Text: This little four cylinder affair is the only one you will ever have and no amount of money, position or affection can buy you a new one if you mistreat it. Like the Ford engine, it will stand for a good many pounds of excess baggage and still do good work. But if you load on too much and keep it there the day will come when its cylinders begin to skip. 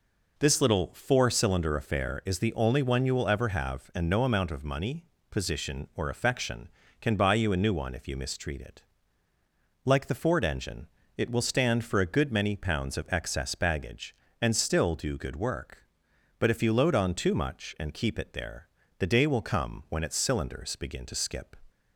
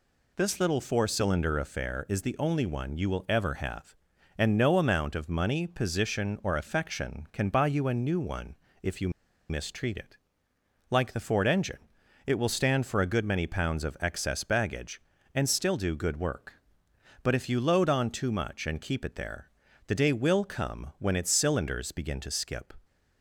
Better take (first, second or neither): first